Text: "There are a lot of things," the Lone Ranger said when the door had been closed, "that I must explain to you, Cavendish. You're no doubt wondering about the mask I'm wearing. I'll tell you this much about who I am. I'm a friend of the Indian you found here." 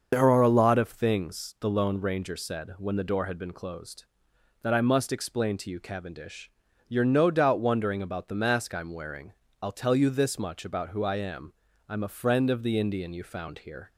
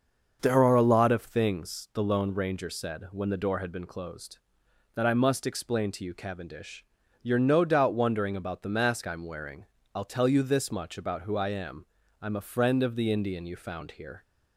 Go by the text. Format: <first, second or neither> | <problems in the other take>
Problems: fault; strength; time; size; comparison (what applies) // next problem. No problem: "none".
second | loses the start of "There"; at 0.1 s; 45 ms // starts louder than the rest; until 1.1 s; 6.5 dB; also in the second